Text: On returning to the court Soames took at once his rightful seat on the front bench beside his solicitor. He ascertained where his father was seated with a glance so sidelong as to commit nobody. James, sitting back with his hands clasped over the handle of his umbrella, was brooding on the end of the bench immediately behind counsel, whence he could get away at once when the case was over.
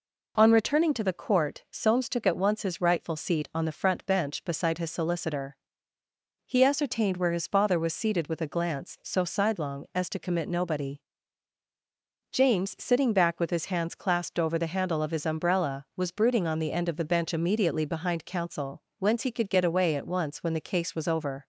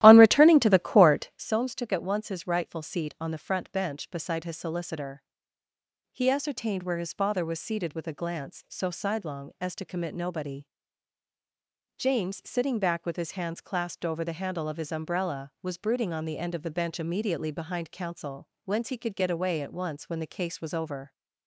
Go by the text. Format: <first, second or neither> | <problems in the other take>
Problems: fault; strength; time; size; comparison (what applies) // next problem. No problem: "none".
first | starts louder than the rest; strong; until 1.5 s; 14.5 dB